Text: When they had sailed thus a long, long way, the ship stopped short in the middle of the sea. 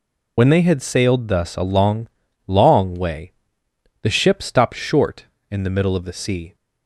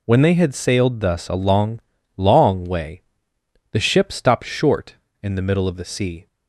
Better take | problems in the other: second | loses the start of "When"; at 0.3 s; 50 ms

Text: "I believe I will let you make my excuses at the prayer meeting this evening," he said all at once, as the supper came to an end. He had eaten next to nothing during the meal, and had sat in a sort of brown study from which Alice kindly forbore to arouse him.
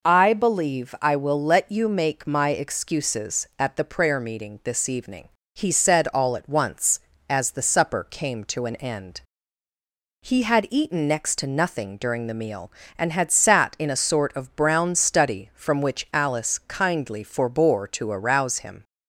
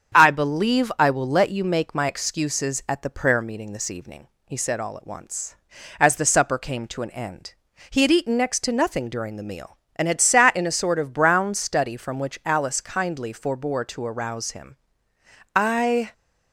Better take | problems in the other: first | starts louder than the rest; strong; until 1.2 s; 7.5 dB // goes on to say "I"; from 15.5 s on; 0.58 s long

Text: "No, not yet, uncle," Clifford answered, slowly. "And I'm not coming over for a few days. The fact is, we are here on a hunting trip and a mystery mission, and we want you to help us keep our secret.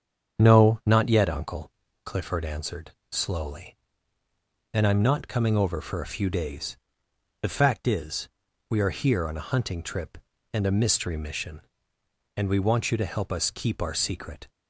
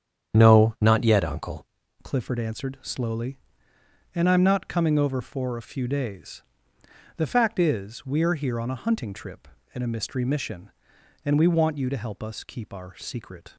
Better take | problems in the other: first | starts louder than the rest; strong; until 1.3 s; 8.5 dB; strong in the first // changes voice at "Clifford"; from 2.0 s on; 11.5 s long

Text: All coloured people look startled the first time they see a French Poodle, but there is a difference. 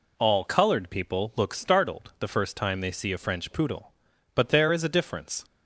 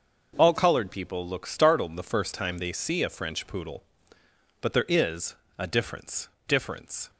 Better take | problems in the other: first | pauses between "is" and "a"; slight; at 5.3 s; 0.24 s long // says "difference" twice; at 6.4 s

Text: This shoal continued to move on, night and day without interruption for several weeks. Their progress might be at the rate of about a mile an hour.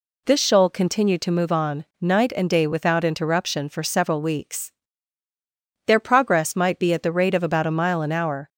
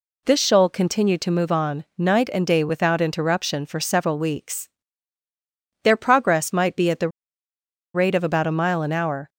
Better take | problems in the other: first | pauses between "the" and "rate"; noticeable; at 7.0 s; 0.85 s long

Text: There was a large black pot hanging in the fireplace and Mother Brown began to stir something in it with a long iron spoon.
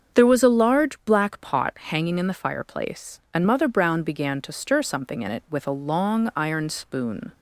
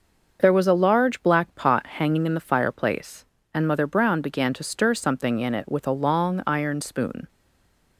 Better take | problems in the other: first | starts louder than the rest; noticeable; until 1.4 s; 6 dB; also in the first // stays silent after the last word; slight; from 7.2 s on; 0.7 s long

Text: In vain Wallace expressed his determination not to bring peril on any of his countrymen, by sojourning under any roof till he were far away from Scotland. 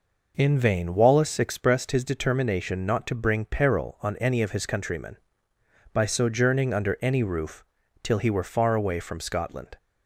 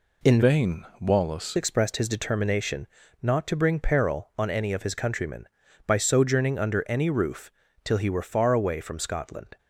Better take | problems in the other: first | changes voice from "vain" to "Wallace"; from 0.4 to 1.5 s; 1.1 s long // pauses between "determination" and "not"; slight; at 2.8 s; 0.34 s long // pauses between "roof" and "till"; slight; at 7.5 s; 0.32 s long; also in the first

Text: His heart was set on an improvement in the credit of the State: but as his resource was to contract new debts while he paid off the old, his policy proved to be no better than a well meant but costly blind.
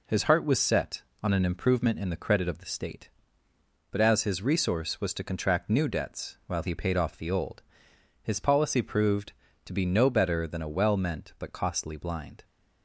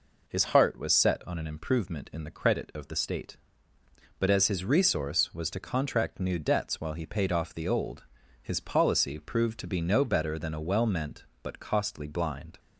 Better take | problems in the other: second | gets quieter; noticeable; throughout; 4 dB

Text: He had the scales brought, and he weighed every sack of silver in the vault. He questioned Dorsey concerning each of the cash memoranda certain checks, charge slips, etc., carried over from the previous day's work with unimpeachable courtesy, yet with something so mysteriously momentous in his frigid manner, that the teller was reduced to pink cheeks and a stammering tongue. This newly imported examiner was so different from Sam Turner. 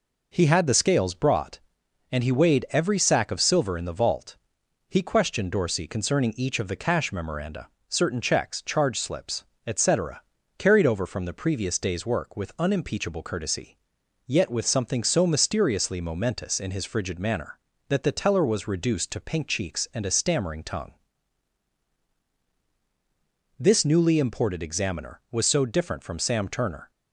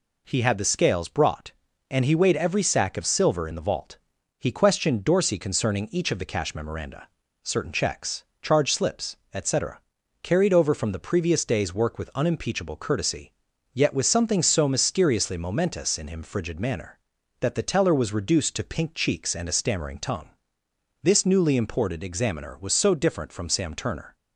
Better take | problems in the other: first | pauses between "memoranda" and "certain"; slight; at 7.0 s; 0.36 s long; slight in the first // says "him" for "his"; at 16.0 s

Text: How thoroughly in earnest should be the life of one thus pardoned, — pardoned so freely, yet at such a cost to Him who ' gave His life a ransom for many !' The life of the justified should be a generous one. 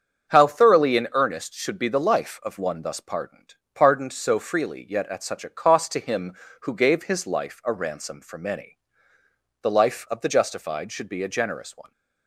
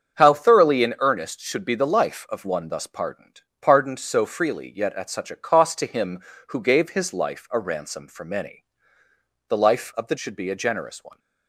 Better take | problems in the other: first | starts louder than the rest; strong; until 1.2 s; 7.5 dB; strong in the first // skips "justified"; at 10.1 s

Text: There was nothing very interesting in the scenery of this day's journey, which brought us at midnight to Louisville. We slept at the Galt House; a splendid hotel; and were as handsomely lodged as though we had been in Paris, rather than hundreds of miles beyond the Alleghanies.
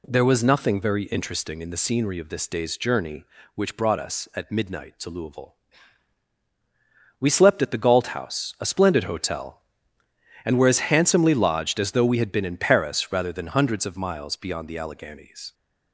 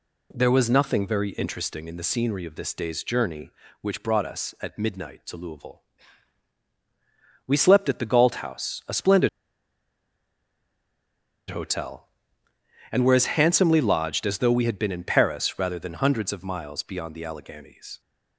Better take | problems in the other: first | pauses between "splendid" and "hotel"; strong; at 9.2 s; 2.2 s long

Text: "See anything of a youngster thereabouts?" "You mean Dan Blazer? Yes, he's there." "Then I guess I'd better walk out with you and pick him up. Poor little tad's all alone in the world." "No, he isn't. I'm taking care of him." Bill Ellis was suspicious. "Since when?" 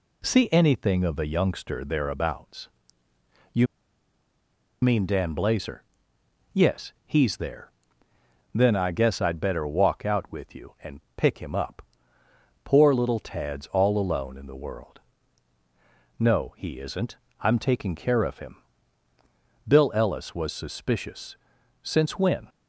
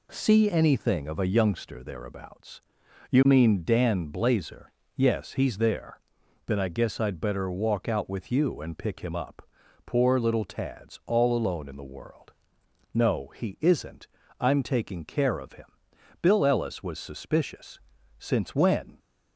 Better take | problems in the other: second | pauses between "You" and "mean"; at 3.6 s; 1.1 s long // pauses between "and" and "pick"; slight; at 10.9 s; 0.16 s long

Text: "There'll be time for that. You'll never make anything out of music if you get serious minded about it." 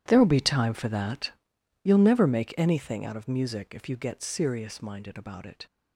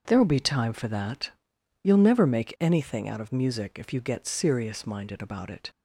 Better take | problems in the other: second | gets quieter; strong; throughout; 17 dB // starts louder than the rest; strong; until 1.0 s; 11 dB; also in the second

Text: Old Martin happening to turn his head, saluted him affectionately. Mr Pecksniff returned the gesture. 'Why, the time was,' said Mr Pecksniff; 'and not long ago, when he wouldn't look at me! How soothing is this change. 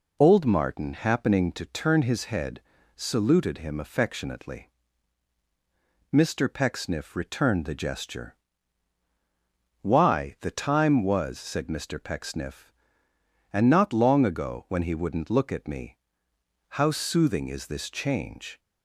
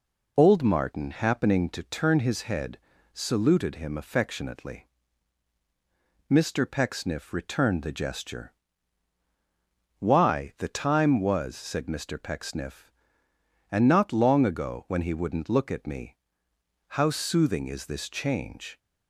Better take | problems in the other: neither | none

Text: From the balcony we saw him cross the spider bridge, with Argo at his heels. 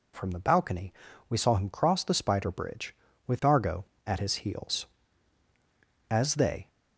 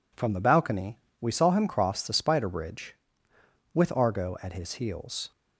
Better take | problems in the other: second | pauses between "balcony" and "we"; slight; at 0.9 s; 0.36 s long; slight in the second // goes on to say "As they"; from 6.0 s on; 0.60 s long

